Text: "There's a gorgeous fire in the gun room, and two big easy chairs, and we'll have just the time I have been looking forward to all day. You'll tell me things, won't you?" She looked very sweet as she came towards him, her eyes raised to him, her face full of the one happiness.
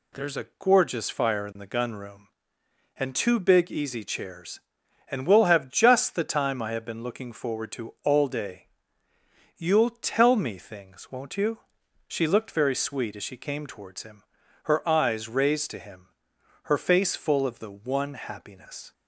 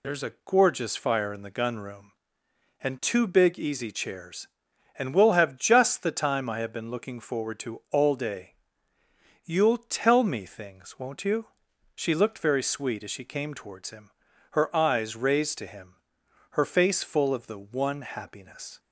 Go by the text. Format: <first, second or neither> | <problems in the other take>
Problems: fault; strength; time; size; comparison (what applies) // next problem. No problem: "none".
first | loses the start of "There's"; at 0.0 s; 45 ms